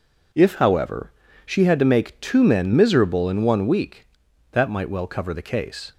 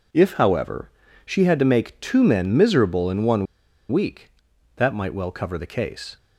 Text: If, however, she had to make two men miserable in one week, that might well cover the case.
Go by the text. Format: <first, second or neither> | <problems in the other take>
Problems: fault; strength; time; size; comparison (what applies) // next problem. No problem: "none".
first | pauses between "one" and "week"; at 3.4 s; 0.44 s long